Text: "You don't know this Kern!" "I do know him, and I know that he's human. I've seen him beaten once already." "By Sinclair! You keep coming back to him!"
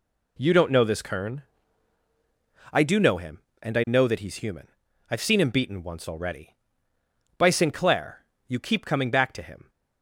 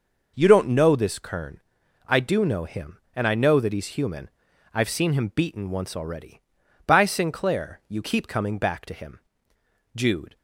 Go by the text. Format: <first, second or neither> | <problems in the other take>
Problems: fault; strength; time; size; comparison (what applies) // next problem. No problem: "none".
first | goes on to say "Jude"; slight; from 9.9 s on; 0.42 s long